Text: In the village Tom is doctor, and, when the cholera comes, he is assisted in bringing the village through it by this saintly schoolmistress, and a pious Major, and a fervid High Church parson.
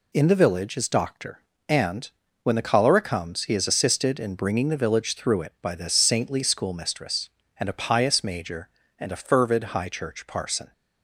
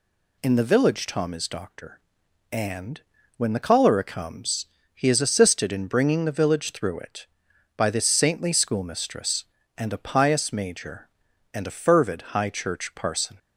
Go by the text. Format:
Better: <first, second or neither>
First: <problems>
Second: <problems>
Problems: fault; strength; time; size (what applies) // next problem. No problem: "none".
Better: second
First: skips "Tom"; at 0.7 s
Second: none